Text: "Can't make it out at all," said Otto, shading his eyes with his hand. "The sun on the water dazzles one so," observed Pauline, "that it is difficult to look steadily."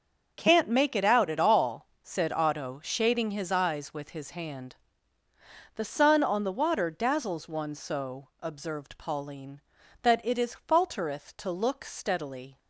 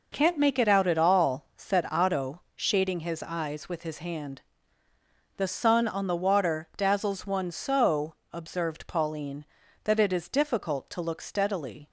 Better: second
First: starts louder than the rest; until 1.3 s; 6.5 dB // says "faltereth" for "difficult"; at 10.5 s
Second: none

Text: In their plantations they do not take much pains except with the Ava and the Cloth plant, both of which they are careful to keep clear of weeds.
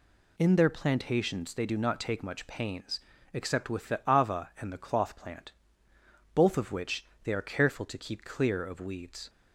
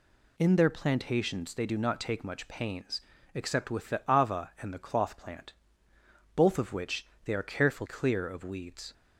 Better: first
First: pauses between "pains" and "except"; slight; at 3.0 s; 0.32 s long // pauses between "which" and "they"; slight; at 7.0 s; 0.20 s long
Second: pauses between "pains" and "except"; slight; at 3.0 s; 0.32 s long // pauses between "which" and "they"; slight; at 7.0 s; 0.20 s long // skips "to keep"; at 7.8 s

